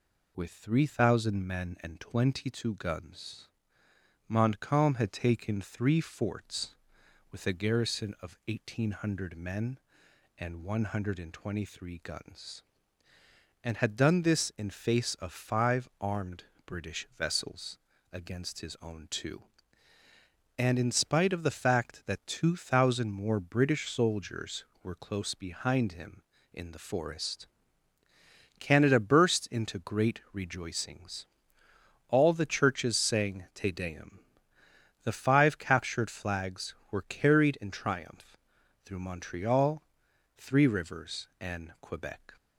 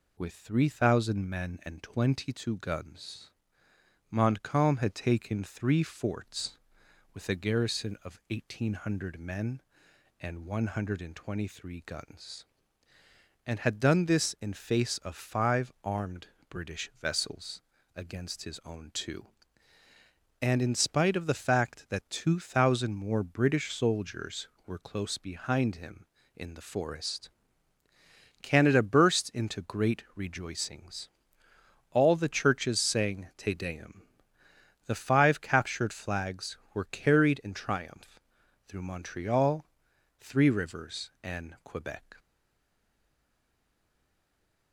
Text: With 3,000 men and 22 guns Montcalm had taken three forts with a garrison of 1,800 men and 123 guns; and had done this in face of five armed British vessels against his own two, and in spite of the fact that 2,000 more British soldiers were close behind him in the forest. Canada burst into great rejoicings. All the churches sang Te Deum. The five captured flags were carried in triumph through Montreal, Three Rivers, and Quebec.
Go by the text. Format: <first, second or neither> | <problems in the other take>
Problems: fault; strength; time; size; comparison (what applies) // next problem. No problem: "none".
first | pauses between "guns" and "Montcalm"; noticeable; at 3.2 s; 0.80 s long; noticeable in the first // pauses between "armed" and "British"; slight; at 16.2 s; 0.20 s long; slight in the first // pauses between "vessels" and "against"; slight; at 17.6 s; 0.34 s long; slight in the first // pauses between "triumph" and "through"; noticeable; at 38.2 s; 0.48 s long; noticeable in the first // stays silent after the last word; strong; from 42.1 s on; 2.6 s long